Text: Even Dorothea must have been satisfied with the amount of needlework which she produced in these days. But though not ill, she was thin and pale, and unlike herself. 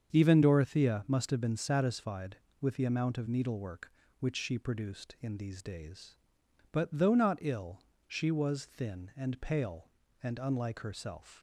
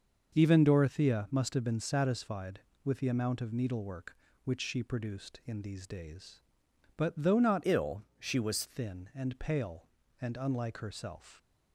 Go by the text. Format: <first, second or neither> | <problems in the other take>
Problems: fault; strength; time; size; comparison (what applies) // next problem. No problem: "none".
first | starts louder than the rest; until 1.3 s; 6.5 dB; strong in the first // changes voice from "ill" to "was"; from 7.6 to 8.6 s; 1.0 s long